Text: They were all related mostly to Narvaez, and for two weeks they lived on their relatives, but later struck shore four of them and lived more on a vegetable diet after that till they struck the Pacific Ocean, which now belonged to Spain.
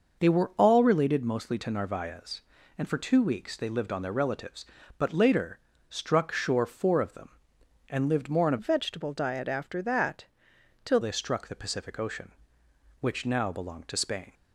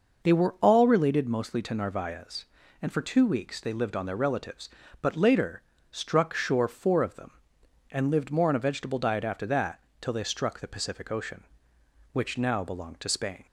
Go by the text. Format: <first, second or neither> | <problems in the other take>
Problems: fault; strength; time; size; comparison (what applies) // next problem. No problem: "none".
second | pauses between "later" and "struck"; slight; at 5.5 s; 0.30 s long; slight in the second // changes voice from "vegetable" to "till"; from 8.5 to 10.9 s; 2.4 s long // pauses between "that" and "till"; noticeable; at 10.2 s; 0.60 s long; slight in the second